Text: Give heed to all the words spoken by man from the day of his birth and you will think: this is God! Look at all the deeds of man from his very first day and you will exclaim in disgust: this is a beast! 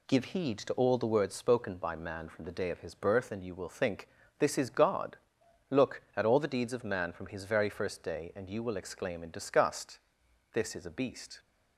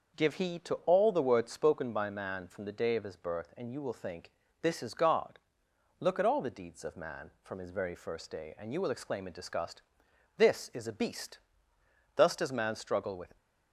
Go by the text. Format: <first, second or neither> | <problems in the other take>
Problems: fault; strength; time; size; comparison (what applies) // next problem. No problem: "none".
first | starts louder than the rest; until 1.3 s; 6 dB // goes on to say "Thus does man struggle with"; noticeable; from 12.1 s on; 1.2 s long